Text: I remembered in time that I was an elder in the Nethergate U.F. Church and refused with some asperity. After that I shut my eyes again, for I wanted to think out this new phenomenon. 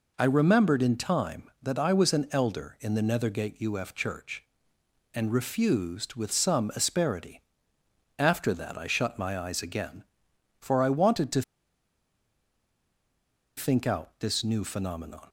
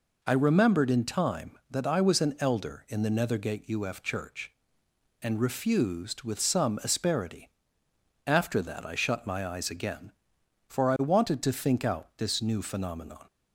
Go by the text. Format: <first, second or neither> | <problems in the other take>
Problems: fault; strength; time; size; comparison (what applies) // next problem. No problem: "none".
second | pauses between "to" and "think"; strong; at 11.4 s; 2.1 s long